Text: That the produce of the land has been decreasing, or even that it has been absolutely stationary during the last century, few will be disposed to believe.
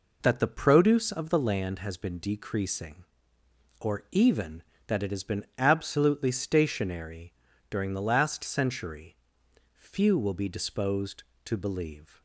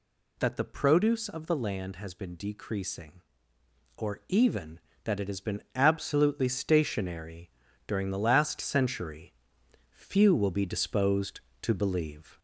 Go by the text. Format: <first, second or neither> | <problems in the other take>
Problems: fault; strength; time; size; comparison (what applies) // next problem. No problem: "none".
first | gets louder; slight; throughout; 2 dB // pauses between "stationary" and "during"; at 7.4 s; 0.40 s long; also in the first